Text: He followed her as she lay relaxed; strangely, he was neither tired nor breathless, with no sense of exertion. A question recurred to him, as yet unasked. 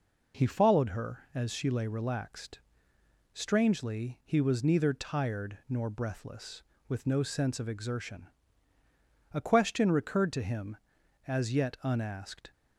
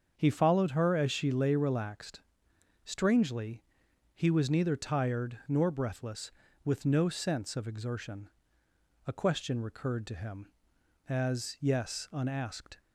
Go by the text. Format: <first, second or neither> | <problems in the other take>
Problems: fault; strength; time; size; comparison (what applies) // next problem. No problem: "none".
first | starts louder than the rest; until 1.1 s; 7 dB // says "yes" for "yet"; at 11.6 s